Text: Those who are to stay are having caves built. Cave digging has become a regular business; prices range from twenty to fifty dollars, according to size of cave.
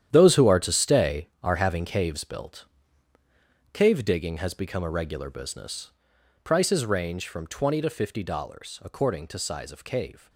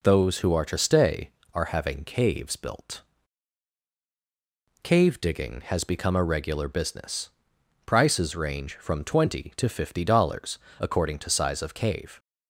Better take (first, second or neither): second